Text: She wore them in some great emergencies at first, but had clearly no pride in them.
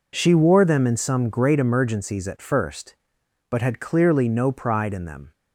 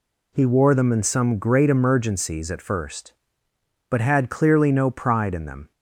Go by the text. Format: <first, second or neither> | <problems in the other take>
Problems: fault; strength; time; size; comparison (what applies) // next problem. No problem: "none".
first | says "He" for "She"; at 0.3 s